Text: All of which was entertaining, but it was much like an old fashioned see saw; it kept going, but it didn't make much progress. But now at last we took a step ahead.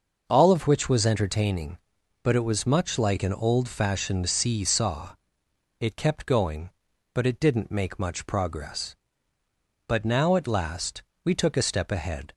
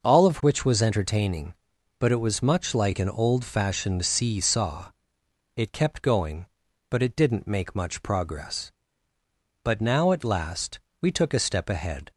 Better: neither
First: pauses between "last" and "we"; slight; at 11.0 s; 0.20 s long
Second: pauses between "last" and "we"; slight; at 10.8 s; 0.20 s long

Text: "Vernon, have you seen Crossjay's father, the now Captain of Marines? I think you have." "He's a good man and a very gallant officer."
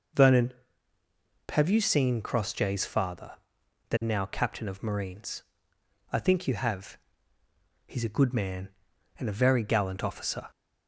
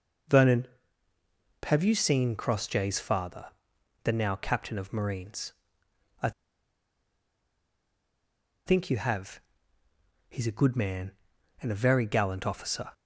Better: first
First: none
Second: pauses between "I" and "think"; strong; at 6.3 s; 2.3 s long

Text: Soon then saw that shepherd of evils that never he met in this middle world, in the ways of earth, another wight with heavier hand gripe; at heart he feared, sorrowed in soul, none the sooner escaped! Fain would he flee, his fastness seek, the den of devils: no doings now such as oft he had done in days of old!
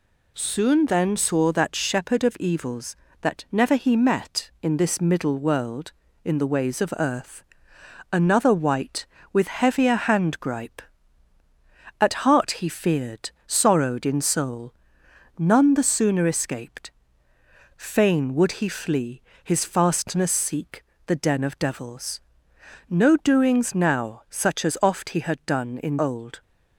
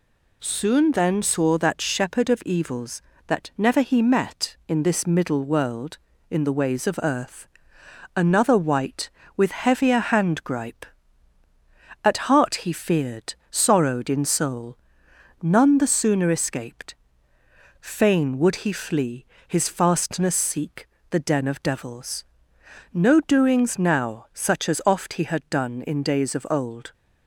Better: second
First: skips "days of"; at 25.9 s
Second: none

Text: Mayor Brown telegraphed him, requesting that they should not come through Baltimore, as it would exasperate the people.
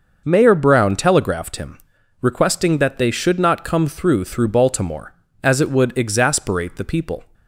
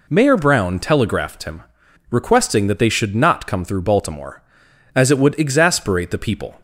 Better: second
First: says "through" twice; at 4.2 s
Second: none

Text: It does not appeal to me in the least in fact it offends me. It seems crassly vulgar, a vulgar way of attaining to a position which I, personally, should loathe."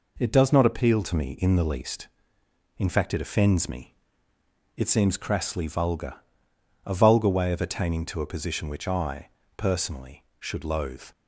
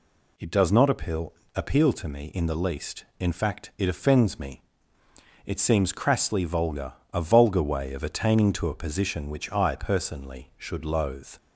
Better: first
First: none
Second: says "appeal" twice; at 1.5 s

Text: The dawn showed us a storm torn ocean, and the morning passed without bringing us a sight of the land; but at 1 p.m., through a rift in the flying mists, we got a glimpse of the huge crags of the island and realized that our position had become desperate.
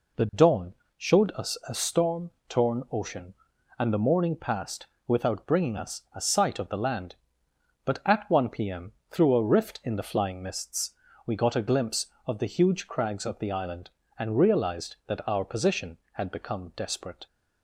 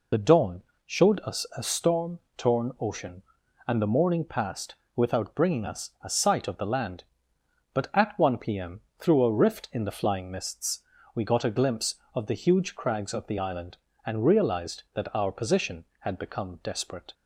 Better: first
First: pauses between "dawn" and "showed"; slight; at 0.7 s; 0.24 s long // pauses between "storm" and "torn"; slight; at 2.3 s; 0.18 s long // pauses between "passed" and "without"; slight; at 4.8 s; 0.20 s long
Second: loses the start of "The"; at 0.1 s; 40 ms // pauses between "dawn" and "showed"; slight; at 0.6 s; 0.24 s long // pauses between "storm" and "torn"; slight; at 2.1 s; 0.18 s long // pauses between "passed" and "without"; slight; at 4.7 s; 0.20 s long

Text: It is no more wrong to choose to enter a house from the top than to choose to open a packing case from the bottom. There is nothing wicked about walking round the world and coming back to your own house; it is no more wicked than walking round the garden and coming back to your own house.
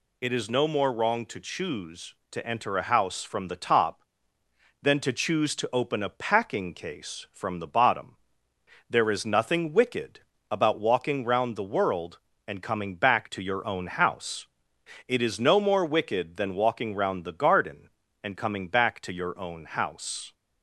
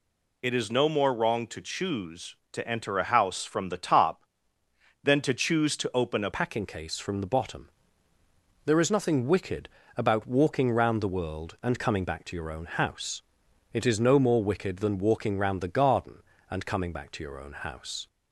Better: first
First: pauses between "wicked" and "about"; slight; at 10.2 s; 0.30 s long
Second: changes voice at "packing"; from 6.3 s on; 11.7 s long // pauses between "wicked" and "about"; slight; at 9.6 s; 0.30 s long

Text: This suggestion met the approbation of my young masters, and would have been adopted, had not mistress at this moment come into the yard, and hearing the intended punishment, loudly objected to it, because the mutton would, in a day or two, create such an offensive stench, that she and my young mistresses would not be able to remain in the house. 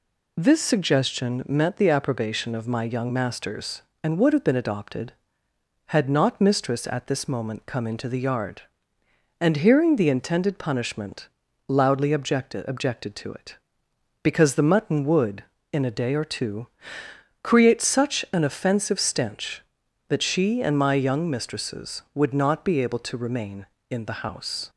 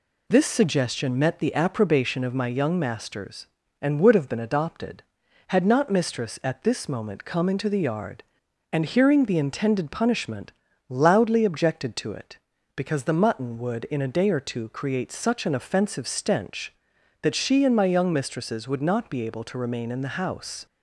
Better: second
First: says "objected" twice; at 12.6 s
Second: none

